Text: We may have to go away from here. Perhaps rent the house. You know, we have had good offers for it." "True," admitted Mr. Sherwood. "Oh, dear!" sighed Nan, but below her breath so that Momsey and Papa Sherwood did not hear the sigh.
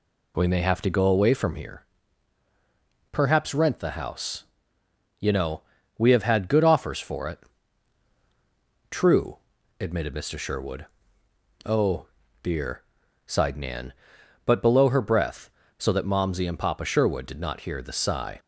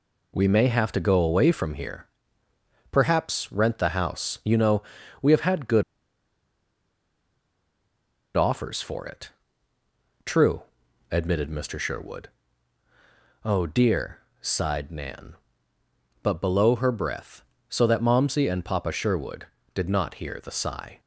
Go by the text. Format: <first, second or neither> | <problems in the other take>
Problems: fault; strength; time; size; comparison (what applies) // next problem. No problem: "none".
first | pauses between "good" and "offers"; strong; at 5.8 s; 2.5 s long